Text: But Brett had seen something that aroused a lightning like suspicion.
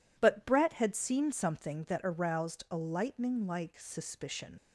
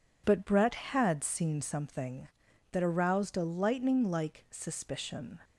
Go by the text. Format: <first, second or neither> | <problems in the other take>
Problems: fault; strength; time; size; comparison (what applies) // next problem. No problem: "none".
second | leaves "suspicion" unfinished; at 4.5 s; 70 ms